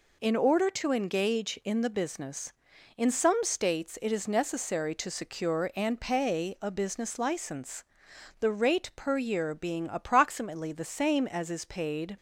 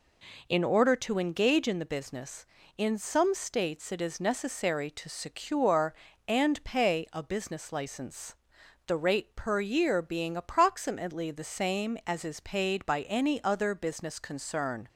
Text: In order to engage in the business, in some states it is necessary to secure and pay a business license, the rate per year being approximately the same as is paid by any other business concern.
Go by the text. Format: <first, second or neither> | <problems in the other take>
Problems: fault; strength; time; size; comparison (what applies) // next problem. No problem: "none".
second | stops before "by any other business concern"; at 12.1 s